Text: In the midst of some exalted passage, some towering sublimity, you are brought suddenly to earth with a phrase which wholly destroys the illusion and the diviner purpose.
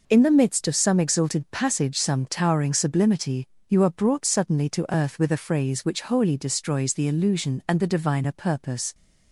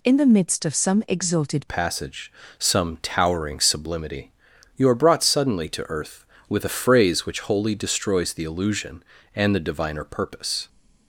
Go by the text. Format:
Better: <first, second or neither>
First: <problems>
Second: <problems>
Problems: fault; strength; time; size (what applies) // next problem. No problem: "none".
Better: first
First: none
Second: changes voice at "passage"; from 1.6 s on; 9.0 s long